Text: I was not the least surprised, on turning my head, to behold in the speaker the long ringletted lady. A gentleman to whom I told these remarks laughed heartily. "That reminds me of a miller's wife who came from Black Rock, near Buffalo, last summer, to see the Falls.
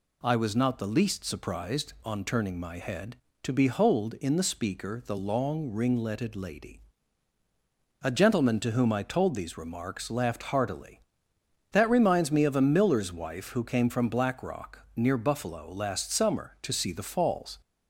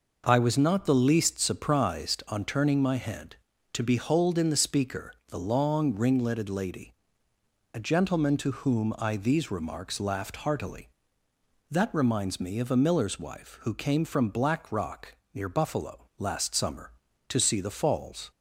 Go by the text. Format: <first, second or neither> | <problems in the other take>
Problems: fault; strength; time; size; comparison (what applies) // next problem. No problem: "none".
first | pauses between "speaker" and "the"; slight; at 5.1 s; 0.16 s long // skips "told"; at 9.1 s